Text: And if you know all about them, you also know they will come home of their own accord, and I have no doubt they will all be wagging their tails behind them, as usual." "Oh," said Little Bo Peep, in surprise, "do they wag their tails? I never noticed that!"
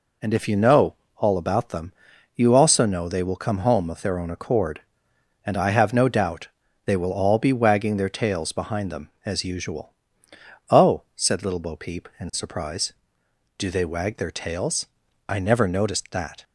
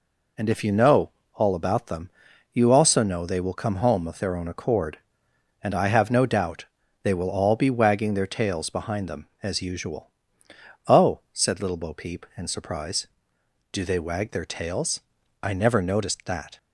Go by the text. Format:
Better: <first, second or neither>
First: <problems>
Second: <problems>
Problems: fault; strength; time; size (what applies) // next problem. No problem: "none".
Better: neither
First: pauses between "know" and "all"; slight; at 0.9 s; 0.24 s long // pauses between "doubt" and "they"; slight; at 6.4 s; 0.36 s long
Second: pauses between "know" and "all"; slight; at 1.0 s; 0.25 s long // pauses between "doubt" and "they"; slight; at 6.6 s; 0.36 s long